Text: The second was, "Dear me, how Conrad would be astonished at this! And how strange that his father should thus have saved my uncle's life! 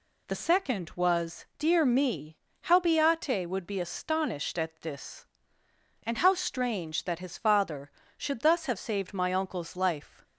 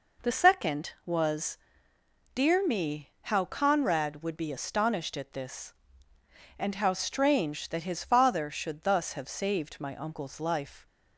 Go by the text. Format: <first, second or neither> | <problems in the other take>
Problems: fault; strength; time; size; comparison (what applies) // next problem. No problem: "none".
second | says "Beate" for "Conrad"; at 2.7 s